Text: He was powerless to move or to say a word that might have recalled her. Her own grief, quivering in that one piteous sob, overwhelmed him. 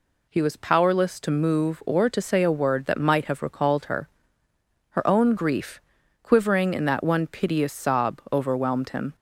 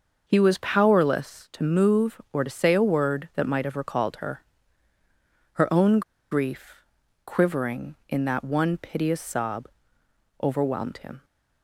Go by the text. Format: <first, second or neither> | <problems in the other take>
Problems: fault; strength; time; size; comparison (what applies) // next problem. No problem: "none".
first | starts louder than the rest; until 1.2 s; 6 dB // pauses between "own" and "grief"; slight; at 6.0 s; 0.30 s long